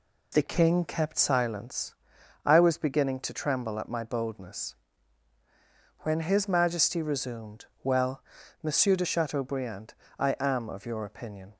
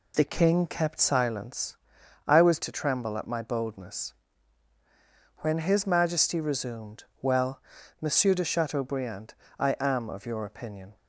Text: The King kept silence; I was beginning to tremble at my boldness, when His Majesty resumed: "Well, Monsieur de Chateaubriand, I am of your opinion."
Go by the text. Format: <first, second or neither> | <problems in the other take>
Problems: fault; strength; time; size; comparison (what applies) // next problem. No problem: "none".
first | skips "beginning"; at 2.6 s